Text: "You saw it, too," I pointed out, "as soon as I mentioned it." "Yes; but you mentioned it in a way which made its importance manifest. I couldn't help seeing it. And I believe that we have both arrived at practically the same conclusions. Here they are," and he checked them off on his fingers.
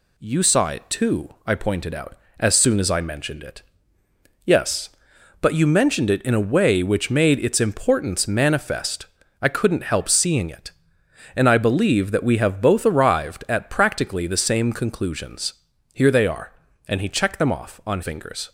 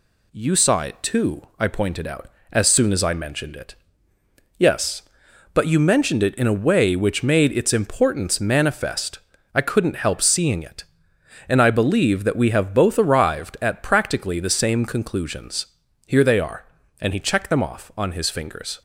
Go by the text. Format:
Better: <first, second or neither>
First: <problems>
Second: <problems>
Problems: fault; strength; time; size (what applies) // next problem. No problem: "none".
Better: second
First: skips "his"; at 18.0 s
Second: none